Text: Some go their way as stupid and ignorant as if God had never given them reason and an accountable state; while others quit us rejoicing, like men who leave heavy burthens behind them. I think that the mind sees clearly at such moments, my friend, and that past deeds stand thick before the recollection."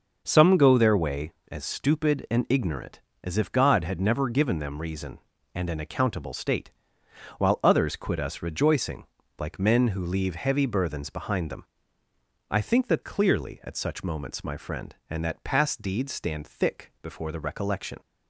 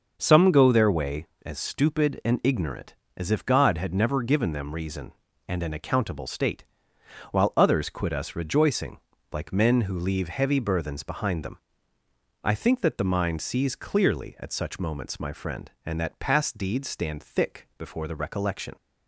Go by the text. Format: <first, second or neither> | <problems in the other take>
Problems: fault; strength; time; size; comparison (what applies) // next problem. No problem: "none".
second | skips "the mind sees"; at 13.0 s